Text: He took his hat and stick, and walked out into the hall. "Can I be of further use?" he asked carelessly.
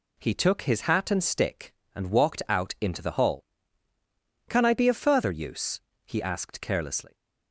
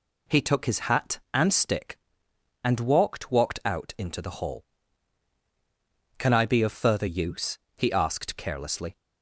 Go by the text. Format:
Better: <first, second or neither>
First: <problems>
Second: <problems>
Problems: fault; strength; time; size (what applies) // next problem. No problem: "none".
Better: first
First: none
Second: says "walked" twice; at 3.3 s